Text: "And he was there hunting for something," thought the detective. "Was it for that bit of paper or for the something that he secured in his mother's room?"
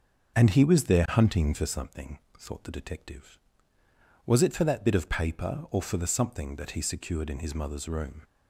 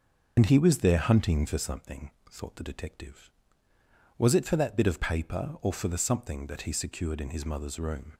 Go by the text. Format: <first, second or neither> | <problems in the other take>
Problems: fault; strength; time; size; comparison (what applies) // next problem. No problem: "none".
first | loses the start of "And"; at 0.3 s; 60 ms // starts louder than the rest; noticeable; until 1.4 s; 6 dB; also in the first